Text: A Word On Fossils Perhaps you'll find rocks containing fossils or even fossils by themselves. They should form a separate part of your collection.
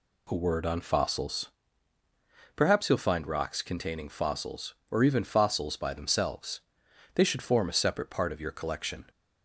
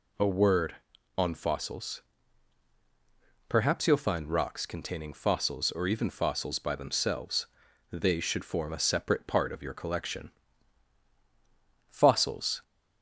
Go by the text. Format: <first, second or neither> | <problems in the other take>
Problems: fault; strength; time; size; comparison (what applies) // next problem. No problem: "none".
first | pauses between "Fossils" and "Perhaps"; strong; at 2.0 s; 1.4 s long; also in the first // goes on to say "Fossils"; noticeable; from 11.9 s on; 0.72 s long